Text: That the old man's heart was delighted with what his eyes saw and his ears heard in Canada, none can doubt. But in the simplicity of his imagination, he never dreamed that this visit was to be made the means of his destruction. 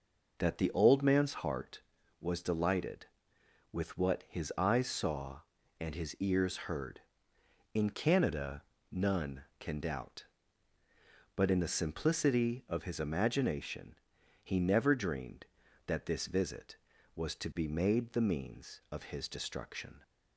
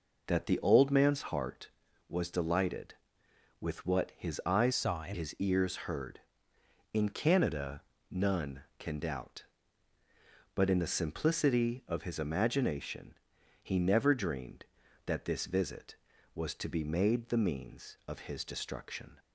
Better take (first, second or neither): first